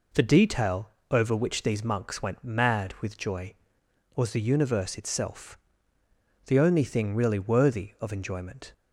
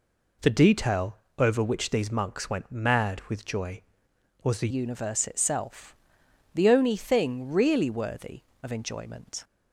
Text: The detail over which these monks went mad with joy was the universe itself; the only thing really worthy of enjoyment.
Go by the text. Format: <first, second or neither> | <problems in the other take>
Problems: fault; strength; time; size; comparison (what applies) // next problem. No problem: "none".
first | pauses between "detail" and "over"; slight; at 1.1 s; 0.20 s long; slight in the first // changes voice at "universe"; from 4.6 s on; 4.8 s long